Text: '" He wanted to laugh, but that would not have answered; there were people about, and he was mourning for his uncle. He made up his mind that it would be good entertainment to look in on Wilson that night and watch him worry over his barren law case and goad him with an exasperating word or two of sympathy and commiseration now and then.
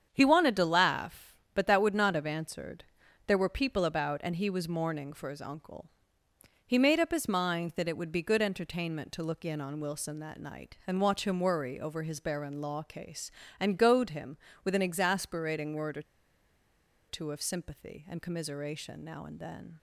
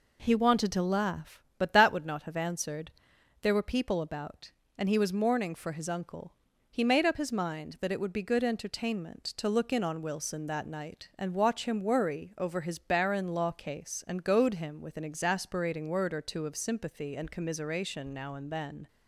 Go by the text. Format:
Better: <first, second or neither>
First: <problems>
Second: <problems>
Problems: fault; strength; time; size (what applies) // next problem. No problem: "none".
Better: second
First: starts louder than the rest; strong; until 1.1 s; 8 dB // pauses between "or" and "two"; at 16.0 s; 1.0 s long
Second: none